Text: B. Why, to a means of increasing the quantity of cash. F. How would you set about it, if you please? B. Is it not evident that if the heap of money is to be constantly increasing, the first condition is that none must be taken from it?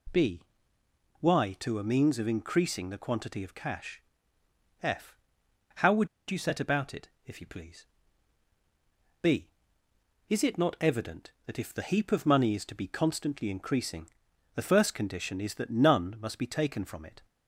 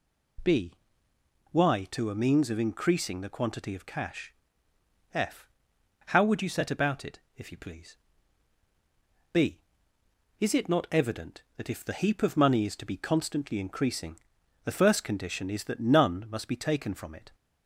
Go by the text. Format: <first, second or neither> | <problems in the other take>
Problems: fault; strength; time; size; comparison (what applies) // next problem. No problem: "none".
second | pauses between "would" and "you"; slight; at 6.0 s; 0.22 s long